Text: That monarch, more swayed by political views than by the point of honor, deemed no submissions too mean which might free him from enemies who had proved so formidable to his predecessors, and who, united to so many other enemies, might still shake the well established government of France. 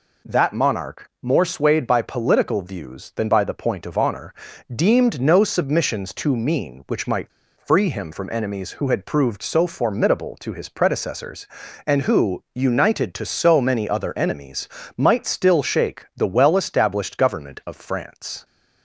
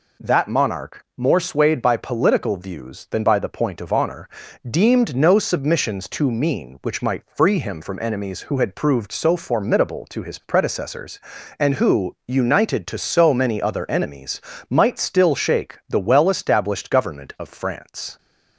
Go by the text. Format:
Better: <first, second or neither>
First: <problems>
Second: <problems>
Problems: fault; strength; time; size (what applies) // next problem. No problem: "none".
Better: second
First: pauses between "might" and "free"; slight; at 7.3 s; 0.28 s long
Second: none